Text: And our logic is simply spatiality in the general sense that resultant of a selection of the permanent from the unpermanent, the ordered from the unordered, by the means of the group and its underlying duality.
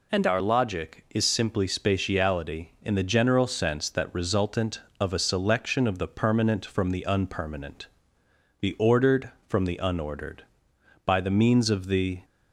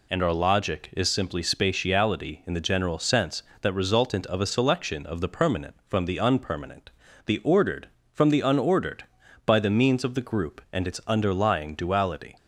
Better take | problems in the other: second | stops before "group and its underlying duality"; at 12.2 s

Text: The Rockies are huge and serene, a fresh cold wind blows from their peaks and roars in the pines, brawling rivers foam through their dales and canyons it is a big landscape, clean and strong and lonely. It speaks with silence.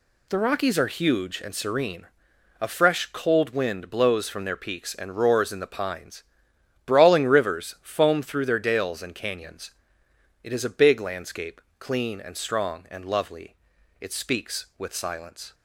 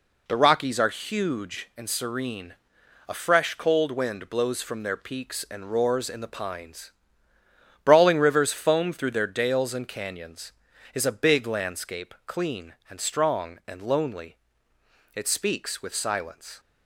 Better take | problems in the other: second | pauses between "canyons" and "it"; noticeable; at 9.7 s; 0.70 s long; also in the second // says "lovely" for "lonely"; at 13.0 s

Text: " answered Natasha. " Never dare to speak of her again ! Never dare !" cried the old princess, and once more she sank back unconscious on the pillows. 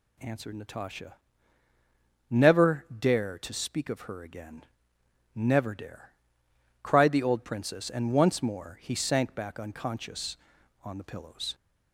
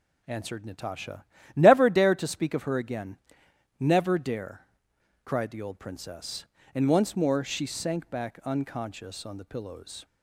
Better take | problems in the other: second | says "he" for "she"; at 8.8 s

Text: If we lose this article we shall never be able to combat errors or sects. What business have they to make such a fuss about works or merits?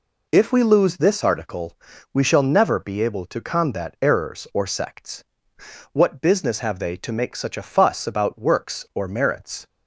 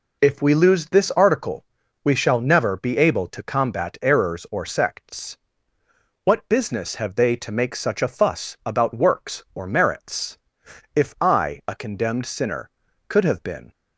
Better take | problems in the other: first | pauses between "article" and "we"; at 1.6 s; 0.40 s long; slight in the first // goes on to say "If I a condemned sinner could have been"; strong; from 10.9 s on; 2.7 s long

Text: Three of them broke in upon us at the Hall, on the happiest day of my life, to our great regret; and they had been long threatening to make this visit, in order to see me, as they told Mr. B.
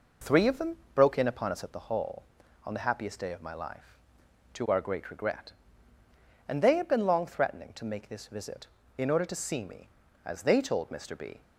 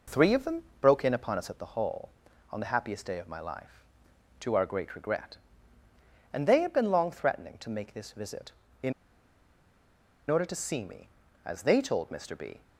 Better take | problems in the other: first | pauses between "them" and "broke"; slight; at 0.6 s; 0.18 s long; slight in the first // pauses between "in" and "order"; strong; at 8.9 s; 1.3 s long

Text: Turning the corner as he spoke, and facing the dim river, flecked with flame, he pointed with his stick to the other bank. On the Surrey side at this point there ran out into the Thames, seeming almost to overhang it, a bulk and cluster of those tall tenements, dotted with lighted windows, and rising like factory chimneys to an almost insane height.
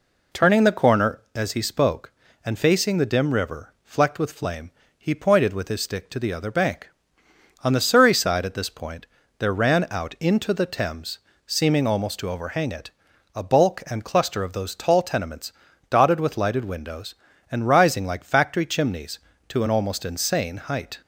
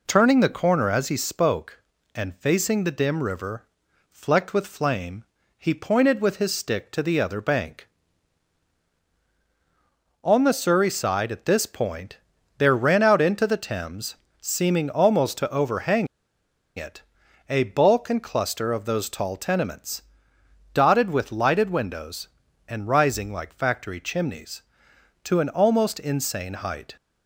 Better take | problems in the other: first | pauses between "point" and "there"; at 12.1 s; 0.40 s long; slight in the first // pauses between "overhang" and "it"; noticeable; at 16.0 s; 0.69 s long

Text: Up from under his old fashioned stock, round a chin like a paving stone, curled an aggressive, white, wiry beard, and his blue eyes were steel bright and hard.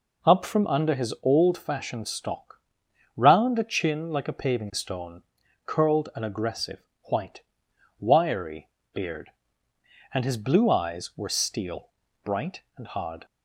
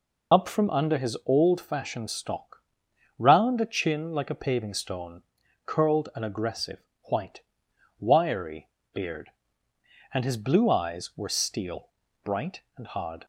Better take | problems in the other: first | loses the start of "Up"; at 0.3 s; 55 ms // pauses between "wiry" and "beard"; slight; at 8.6 s; 0.24 s long; slight in the first // pauses between "steel" and "bright"; slight; at 11.8 s; 0.34 s long; slight in the first

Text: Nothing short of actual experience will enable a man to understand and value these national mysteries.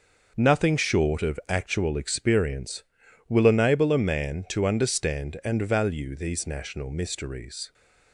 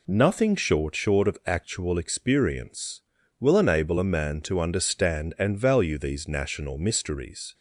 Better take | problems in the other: first | says "short" twice; at 0.9 s

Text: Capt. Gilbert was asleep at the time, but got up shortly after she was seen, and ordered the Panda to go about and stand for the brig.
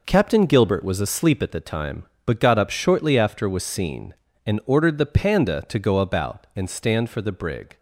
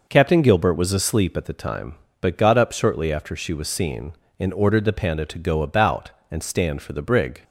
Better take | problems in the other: second | skips "she"; at 3.4 s

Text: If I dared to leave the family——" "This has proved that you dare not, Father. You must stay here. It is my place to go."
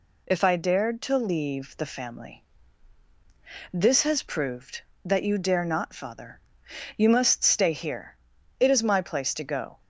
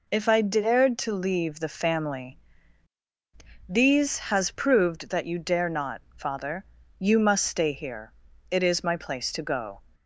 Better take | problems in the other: first | says "These" for "This"; at 3.6 s

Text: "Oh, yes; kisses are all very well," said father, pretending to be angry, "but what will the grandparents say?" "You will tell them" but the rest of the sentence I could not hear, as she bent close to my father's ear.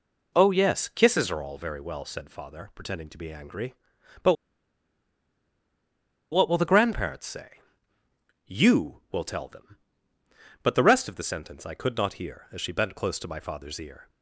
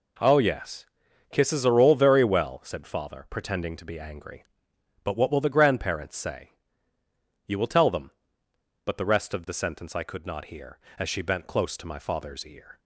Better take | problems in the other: second | pauses between "but" and "what"; strong; at 4.3 s; 1.9 s long

